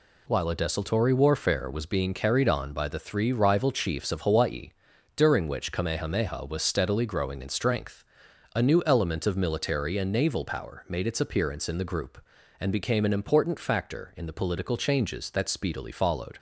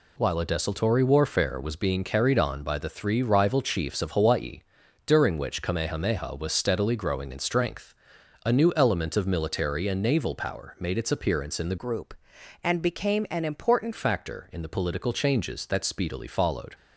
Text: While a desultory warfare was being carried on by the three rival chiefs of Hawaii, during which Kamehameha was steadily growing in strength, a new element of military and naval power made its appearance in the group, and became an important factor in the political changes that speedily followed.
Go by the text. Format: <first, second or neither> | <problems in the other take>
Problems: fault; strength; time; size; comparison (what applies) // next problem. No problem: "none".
first | changes voice from "group" to "important"; from 11.7 to 13.9 s; 2.2 s long